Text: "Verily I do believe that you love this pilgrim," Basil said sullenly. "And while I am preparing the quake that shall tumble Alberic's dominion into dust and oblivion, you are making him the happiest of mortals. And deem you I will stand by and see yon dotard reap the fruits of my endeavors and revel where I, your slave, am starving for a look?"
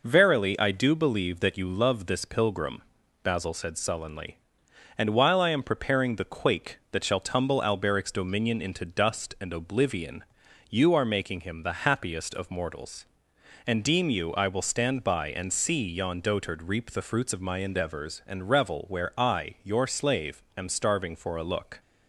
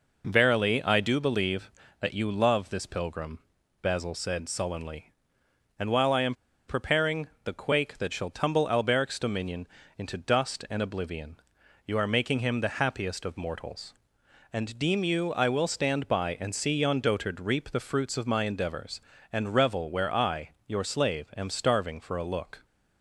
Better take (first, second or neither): first